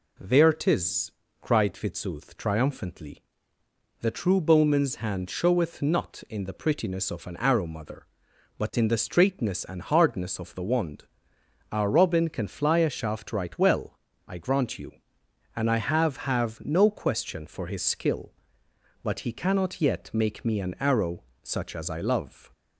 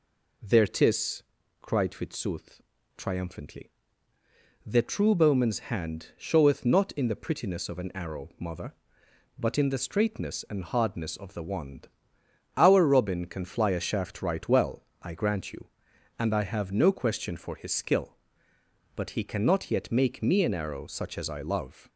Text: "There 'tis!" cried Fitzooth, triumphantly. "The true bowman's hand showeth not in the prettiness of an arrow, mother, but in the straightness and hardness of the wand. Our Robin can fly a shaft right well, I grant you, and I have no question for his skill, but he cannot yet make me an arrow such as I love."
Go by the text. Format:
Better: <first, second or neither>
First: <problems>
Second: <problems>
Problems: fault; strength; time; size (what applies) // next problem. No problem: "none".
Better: second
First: says "have" twice; at 16.1 s // pauses between "arrow" and "such"; slight; at 21.2 s; 0.18 s long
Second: none